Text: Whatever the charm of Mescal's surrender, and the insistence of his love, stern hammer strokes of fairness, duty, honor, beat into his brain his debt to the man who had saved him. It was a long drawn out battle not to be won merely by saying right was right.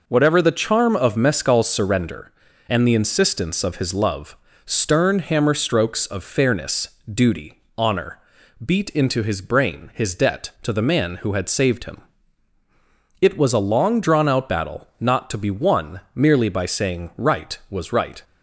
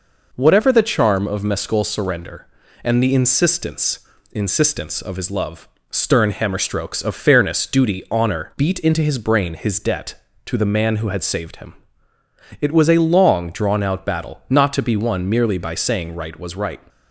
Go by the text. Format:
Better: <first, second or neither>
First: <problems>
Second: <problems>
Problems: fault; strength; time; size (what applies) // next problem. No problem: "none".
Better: first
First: none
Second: says "insistence" twice; at 4.3 s